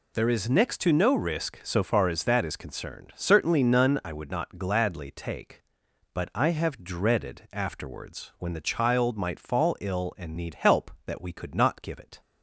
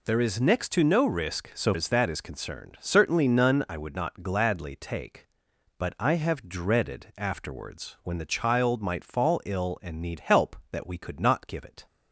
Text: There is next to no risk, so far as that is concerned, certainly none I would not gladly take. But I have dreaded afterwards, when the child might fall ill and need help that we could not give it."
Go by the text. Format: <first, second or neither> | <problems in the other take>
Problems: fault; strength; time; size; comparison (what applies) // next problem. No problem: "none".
first | skips "far"; at 1.7 s